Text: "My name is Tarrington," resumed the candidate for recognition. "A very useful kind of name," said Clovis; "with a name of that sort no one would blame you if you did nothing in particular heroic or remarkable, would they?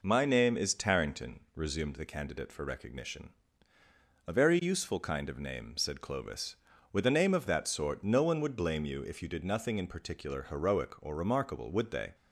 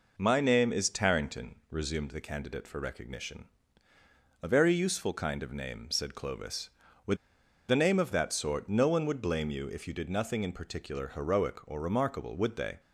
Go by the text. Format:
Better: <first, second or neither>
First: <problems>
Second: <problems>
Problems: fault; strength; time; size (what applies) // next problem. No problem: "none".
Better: first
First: none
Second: pauses between "with" and "a"; noticeable; at 7.1 s; 0.52 s long